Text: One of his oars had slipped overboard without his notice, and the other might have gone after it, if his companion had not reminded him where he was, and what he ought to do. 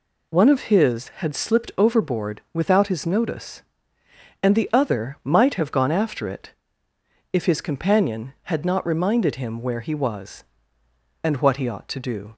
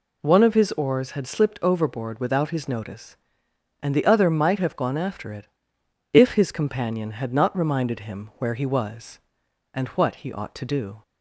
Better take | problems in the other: second | skips "oars"; at 1.0 s

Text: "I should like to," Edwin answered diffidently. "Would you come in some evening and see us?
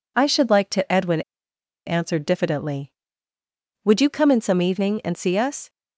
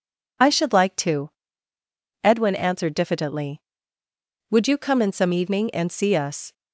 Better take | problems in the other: second | pauses between "Edwin" and "answered"; noticeable; at 1.2 s; 0.65 s long

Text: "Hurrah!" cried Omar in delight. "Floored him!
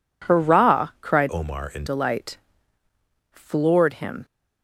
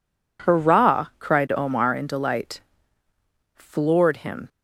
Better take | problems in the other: second | changes voice from "Omar" to "in"; from 1.3 to 1.8 s; 0.5 s long

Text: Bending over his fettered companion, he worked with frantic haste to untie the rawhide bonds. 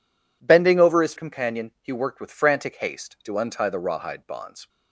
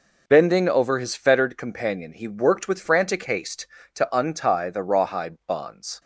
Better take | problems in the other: second | skips "fettered"; at 1.1 s

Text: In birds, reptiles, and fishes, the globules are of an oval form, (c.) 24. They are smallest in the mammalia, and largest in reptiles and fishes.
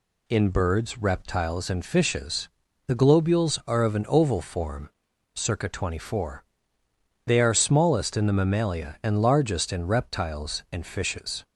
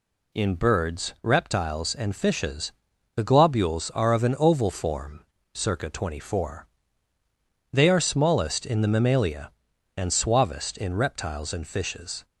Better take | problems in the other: first | says "suavest" for "largest"; at 10.1 s

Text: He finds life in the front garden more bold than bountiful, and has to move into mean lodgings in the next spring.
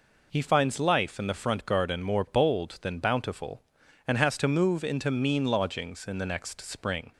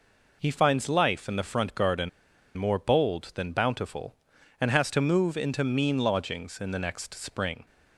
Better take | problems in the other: first | pauses between "garden" and "more"; noticeable; at 2.0 s; 0.47 s long

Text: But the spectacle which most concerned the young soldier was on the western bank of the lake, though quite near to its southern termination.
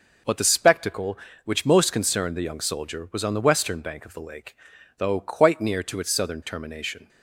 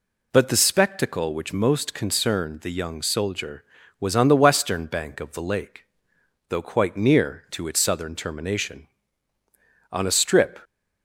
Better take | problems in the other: first | goes on to say "On a strip"; noticeable; from 9.9 s on; 0.68 s long

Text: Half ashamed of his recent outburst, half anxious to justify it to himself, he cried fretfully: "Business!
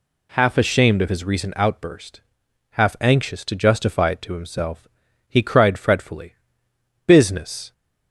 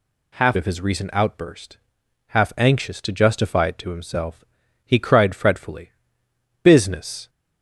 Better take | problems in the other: first | skips "ashamed"; at 0.5 s

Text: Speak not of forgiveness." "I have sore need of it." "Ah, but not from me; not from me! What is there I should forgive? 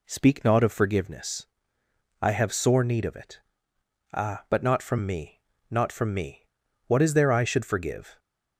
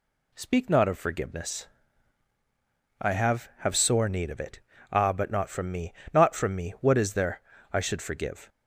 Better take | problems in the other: first | says "have" twice; at 3.5 s // pauses between "there" and "I"; slight; at 7.4 s; 0.30 s long

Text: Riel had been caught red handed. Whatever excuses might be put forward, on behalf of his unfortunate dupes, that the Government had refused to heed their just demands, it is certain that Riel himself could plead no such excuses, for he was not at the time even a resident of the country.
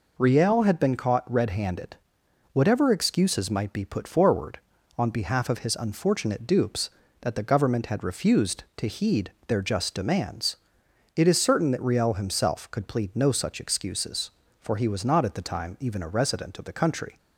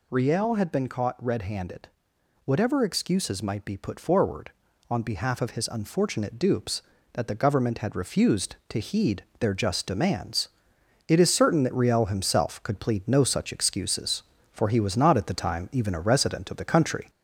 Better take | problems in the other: first | gets louder; slight; throughout; 2.5 dB // pauses between "heed" and "their"; slight; at 9.2 s; 0.16 s long; slight in the first

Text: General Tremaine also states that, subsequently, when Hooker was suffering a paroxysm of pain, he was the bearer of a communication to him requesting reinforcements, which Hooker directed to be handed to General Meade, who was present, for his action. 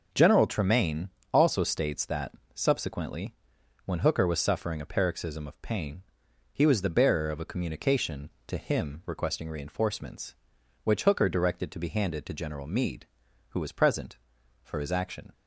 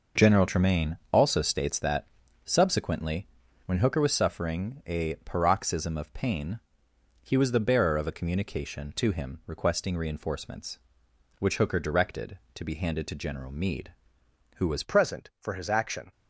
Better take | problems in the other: first | pauses between "Tremaine" and "also"; slight; at 0.9 s; 0.16 s long; slight in the first // changes voice at "present"; from 14.8 s on; 1.3 s long

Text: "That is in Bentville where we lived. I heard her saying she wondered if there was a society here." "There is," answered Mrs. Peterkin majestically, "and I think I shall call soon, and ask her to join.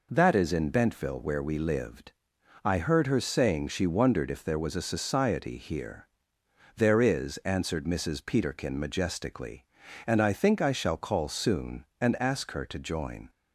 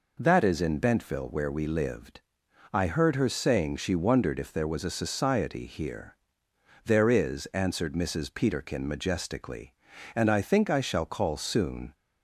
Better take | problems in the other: first | stops before "and ask her to join"; at 11.9 s

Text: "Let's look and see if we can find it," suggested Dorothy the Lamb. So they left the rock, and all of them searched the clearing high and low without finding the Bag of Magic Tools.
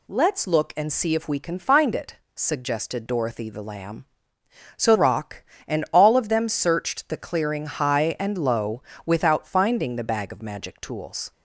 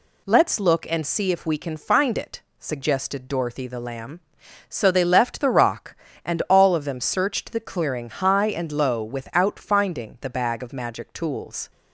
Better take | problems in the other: second | skips "they left the"; at 4.9 s // pauses between "low" and "without"; slight; at 8.8 s; 0.24 s long

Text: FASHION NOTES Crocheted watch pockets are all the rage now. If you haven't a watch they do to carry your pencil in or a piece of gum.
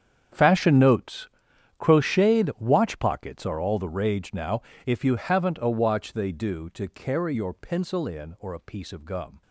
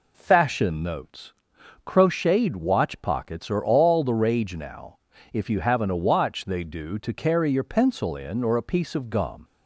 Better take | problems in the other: second | gets quieter; strong; throughout; 17 dB // pauses between "NOTES" and "Crocheted"; noticeable; at 1.2 s; 0.48 s long; noticeable in the second

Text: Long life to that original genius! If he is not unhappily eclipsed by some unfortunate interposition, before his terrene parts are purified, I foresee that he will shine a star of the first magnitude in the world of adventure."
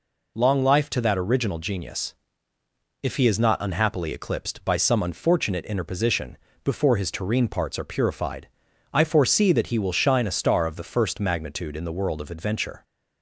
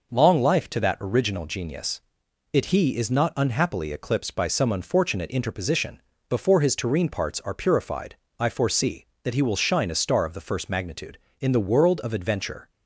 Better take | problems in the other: first | says "It" for "If"; at 2.5 s

